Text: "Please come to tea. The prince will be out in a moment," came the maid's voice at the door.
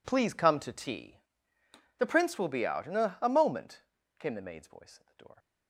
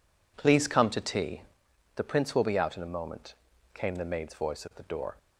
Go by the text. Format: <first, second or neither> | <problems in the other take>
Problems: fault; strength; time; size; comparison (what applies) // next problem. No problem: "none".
second | says "a" twice; at 3.2 s